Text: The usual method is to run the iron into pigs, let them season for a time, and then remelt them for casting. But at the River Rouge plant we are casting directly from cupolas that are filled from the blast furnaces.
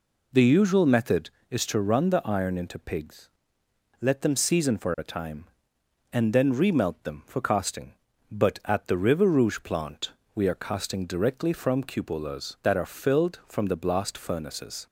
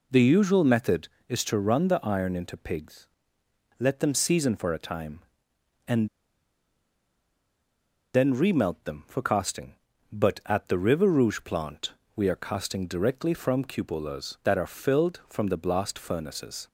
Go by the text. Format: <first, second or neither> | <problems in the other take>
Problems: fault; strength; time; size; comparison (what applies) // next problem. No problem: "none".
first | pauses between "and" and "then"; strong; at 6.0 s; 2.0 s long // pauses between "plant" and "we"; slight; at 11.9 s; 0.24 s long; slight in the first